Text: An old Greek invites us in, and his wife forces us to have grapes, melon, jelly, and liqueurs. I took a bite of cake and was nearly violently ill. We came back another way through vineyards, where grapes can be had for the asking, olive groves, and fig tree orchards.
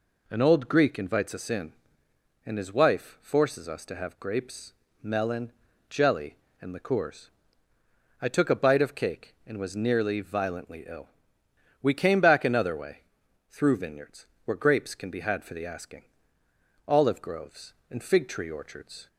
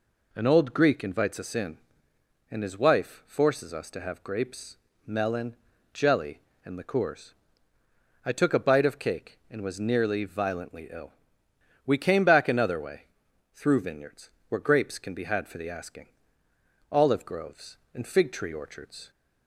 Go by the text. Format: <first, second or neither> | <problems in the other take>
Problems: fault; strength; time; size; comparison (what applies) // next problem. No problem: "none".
neither | pauses between "way" and "through"; noticeable; the same in both